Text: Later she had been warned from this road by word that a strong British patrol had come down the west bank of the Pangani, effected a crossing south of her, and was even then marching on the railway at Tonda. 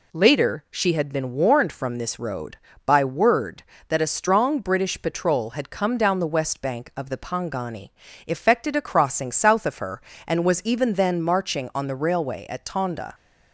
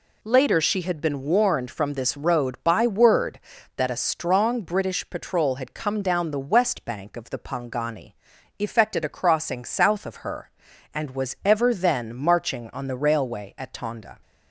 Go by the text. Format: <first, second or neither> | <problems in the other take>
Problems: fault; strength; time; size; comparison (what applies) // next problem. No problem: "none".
first | says "ever" for "even"; at 11.4 s